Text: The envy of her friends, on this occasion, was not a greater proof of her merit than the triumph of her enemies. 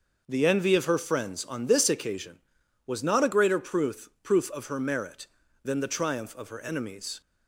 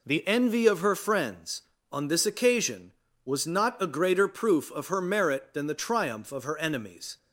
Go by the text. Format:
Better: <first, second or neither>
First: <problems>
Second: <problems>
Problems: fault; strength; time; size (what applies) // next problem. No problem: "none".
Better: second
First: says "proof" twice; at 4.2 s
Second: none